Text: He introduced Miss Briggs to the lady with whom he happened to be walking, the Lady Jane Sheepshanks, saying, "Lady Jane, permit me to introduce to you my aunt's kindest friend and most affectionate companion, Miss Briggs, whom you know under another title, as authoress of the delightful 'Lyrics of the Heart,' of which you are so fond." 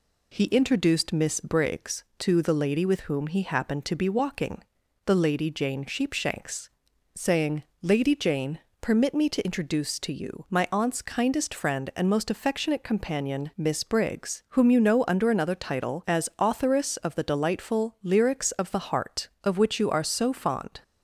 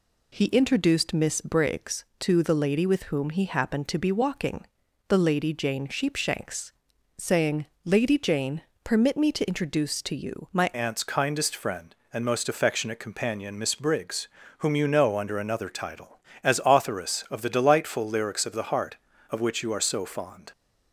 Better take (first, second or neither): first